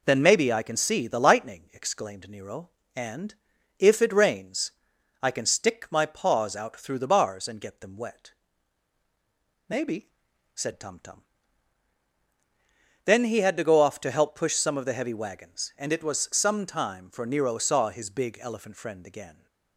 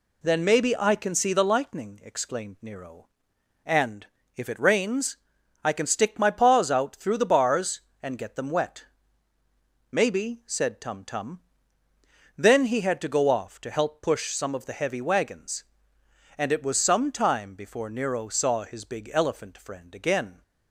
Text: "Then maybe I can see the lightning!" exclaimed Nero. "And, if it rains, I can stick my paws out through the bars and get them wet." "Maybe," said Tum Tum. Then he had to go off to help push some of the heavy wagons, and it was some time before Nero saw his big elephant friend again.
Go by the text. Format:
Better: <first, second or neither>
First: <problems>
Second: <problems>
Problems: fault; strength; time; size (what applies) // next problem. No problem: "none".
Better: second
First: says "for" for "before"; at 17.1 s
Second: none